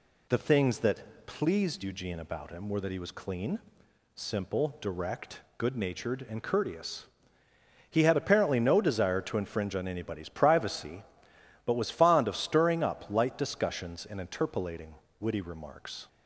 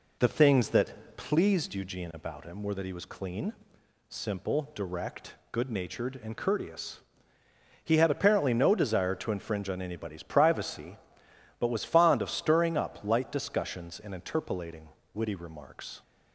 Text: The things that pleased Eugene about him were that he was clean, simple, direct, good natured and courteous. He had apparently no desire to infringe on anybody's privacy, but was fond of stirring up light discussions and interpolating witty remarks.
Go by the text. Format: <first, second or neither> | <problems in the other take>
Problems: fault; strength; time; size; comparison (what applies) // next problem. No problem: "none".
first | starts louder than the rest; slight; until 2.1 s; 3 dB // pauses between "interpolating" and "witty"; slight; at 14.8 s; 0.24 s long; slight in the first